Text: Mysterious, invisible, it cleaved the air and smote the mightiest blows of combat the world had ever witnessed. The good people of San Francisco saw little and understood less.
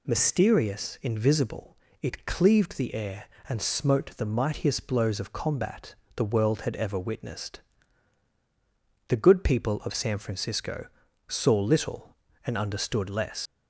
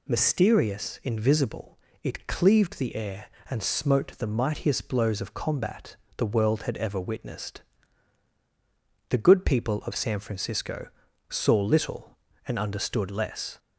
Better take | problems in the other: second | pauses between "combat" and "the"; slight; at 5.9 s; 0.22 s long; slight in the second // pauses between "Francisco" and "saw"; at 10.8 s; 0.40 s long; also in the second // leaves "less" unfinished; at 13.4 s; 115 ms

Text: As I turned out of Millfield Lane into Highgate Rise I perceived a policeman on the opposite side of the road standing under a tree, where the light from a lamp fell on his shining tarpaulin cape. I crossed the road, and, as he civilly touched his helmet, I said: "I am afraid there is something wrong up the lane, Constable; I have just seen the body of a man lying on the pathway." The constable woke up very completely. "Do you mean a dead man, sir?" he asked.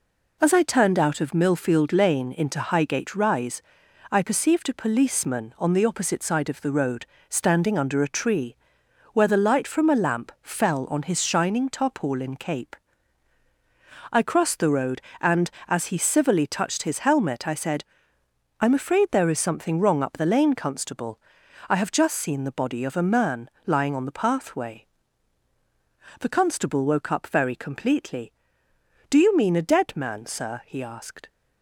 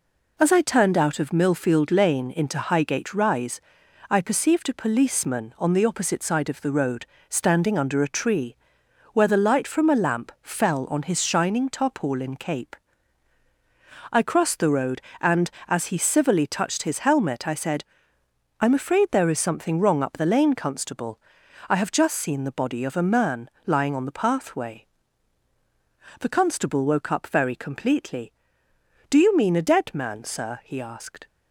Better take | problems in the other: neither | pauses between "Rise" and "I"; noticeable; the same in both // pauses between "road" and "standing"; slight; the same in both // pauses between "man" and "lying"; slight; the same in both

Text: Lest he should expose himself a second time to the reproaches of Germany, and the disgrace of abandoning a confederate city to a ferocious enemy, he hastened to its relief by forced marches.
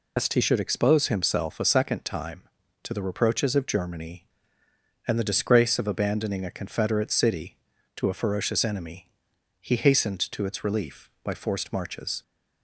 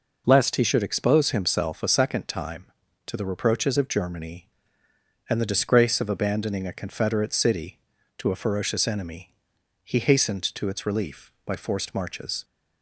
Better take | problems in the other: second | loses the start of "Lest"; at 0.1 s; 125 ms

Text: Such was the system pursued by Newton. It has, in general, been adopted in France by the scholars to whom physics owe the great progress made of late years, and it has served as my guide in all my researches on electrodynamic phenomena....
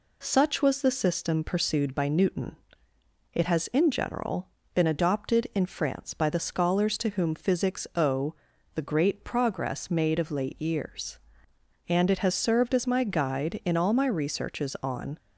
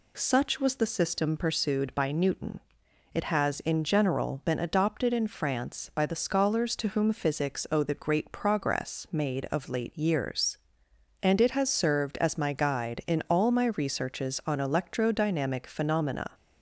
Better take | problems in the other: second | pauses between "owe" and "the"; at 8.3 s; 0.40 s long // stops before "electrodynamic phenomena"; at 15.1 s

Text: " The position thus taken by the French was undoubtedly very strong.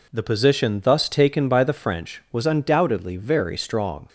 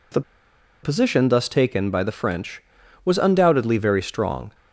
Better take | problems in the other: first | pauses between "The" and "position"; noticeable; at 0.2 s; 0.62 s long

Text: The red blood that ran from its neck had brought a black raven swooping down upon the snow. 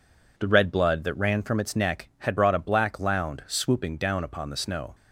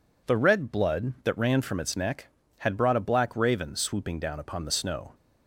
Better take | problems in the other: second | says "lound" for "raven"; at 2.9 s

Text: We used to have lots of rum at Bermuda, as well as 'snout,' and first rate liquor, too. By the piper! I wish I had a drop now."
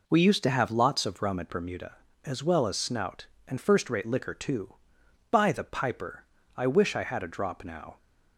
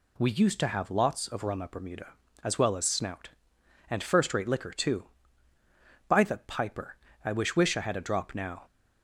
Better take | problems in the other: first | says "wish" twice; at 7.5 s

